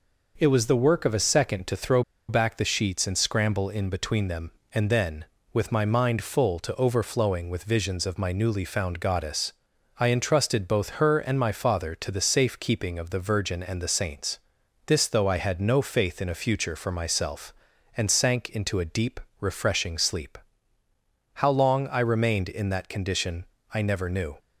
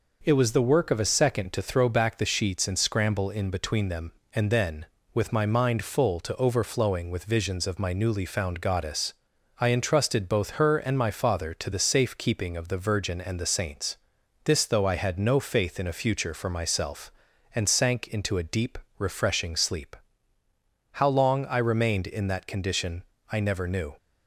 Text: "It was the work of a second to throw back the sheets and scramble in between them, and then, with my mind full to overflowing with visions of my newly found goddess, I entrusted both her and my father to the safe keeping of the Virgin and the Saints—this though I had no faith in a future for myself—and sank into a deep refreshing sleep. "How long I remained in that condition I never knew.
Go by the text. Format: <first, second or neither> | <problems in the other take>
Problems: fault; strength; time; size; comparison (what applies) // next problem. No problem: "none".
second | pauses between "throw" and "back"; slight; at 2.0 s; 0.26 s long // pauses between "deep" and "refreshing"; slight; at 19.1 s; 0.20 s long; slight in the second // pauses between "condition" and "I"; slight; at 23.4 s; 0.28 s long; slight in the second